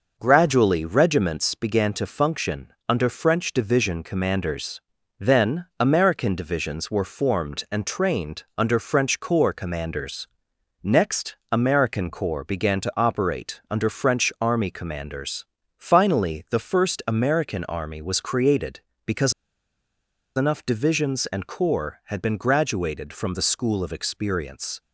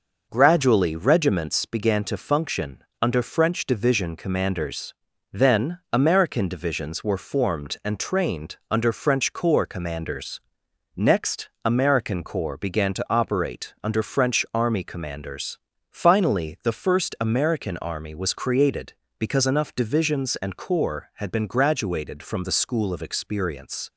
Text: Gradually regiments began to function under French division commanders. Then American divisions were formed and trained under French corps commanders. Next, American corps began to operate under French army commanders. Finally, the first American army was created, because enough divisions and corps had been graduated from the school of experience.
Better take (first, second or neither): second